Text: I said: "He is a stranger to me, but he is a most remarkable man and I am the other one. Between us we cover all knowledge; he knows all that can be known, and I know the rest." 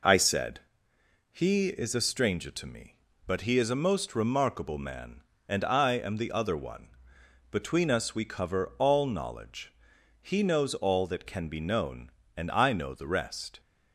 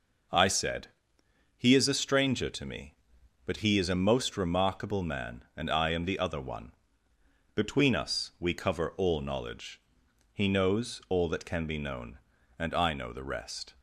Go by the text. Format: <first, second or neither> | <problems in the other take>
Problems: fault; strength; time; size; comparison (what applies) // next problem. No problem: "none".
neither | none